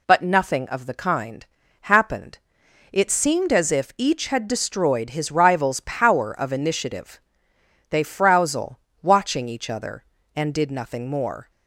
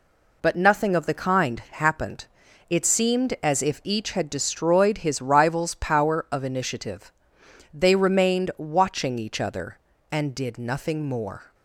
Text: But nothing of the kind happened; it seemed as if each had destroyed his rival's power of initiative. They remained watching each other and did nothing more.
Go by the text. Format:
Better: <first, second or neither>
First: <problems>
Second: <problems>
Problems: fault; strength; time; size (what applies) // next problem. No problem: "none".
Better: second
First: pauses between "kind" and "happened"; slight; at 1.4 s; 0.36 s long // says "frowzle" for "remained"; at 8.0 s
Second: none